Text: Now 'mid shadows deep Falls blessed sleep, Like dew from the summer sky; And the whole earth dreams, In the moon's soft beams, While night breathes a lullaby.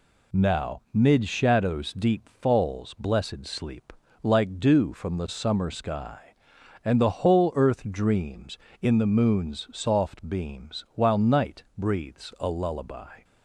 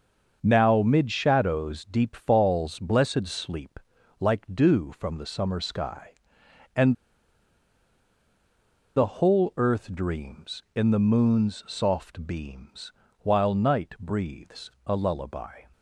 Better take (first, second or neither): first